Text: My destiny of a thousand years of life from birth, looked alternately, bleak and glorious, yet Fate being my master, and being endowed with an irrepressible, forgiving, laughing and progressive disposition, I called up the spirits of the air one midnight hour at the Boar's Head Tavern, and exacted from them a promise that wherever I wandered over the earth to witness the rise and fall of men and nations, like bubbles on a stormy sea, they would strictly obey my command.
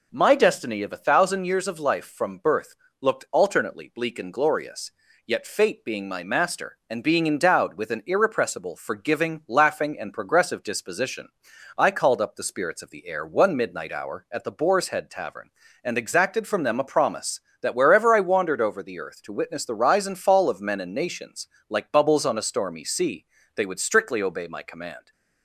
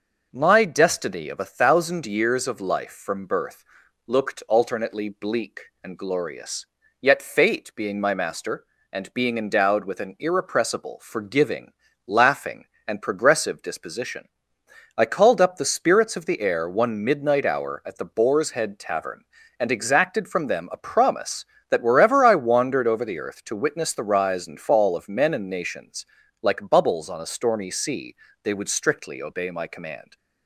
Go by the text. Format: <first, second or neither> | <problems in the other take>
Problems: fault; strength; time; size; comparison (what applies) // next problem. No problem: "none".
neither | none